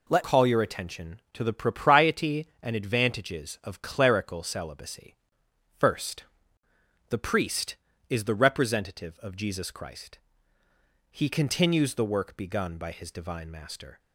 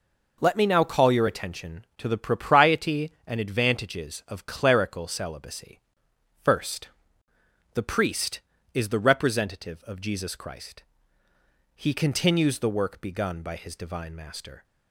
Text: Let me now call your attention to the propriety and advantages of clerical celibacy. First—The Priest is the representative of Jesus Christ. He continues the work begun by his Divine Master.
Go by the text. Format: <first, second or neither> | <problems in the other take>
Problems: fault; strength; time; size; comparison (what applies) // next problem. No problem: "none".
second | skips "me now"; at 0.2 s